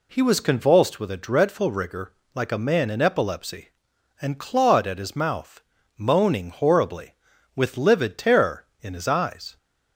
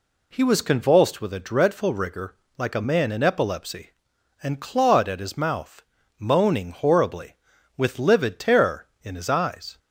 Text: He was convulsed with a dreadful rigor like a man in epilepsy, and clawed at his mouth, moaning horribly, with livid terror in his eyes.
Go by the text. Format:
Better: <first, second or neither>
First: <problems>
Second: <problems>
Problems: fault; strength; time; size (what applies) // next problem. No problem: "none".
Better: neither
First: pauses between "rigor" and "like"; slight; at 2.1 s; 0.21 s long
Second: pauses between "rigor" and "like"; slight; at 2.3 s; 0.22 s long